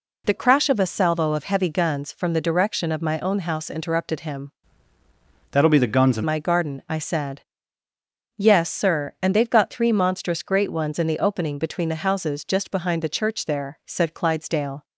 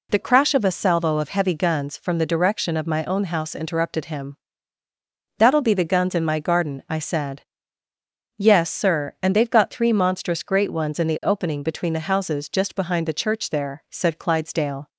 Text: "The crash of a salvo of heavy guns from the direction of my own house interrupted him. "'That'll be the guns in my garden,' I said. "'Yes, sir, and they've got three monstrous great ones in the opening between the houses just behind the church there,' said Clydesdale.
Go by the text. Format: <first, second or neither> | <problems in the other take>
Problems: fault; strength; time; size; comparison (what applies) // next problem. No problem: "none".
second | changes voice from "That'll" to "in"; from 5.5 to 6.2 s; 0.7 s long